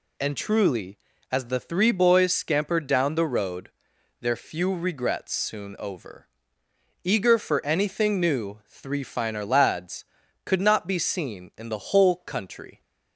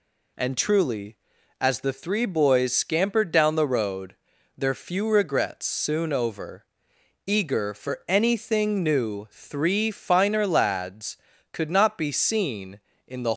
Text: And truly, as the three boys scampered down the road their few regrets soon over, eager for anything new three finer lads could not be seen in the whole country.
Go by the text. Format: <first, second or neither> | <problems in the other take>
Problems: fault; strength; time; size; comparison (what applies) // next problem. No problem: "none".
first | pauses between "road" and "their"; at 4.1 s; 0.40 s long; noticeable in the first // stops before "whole country"; at 13.3 s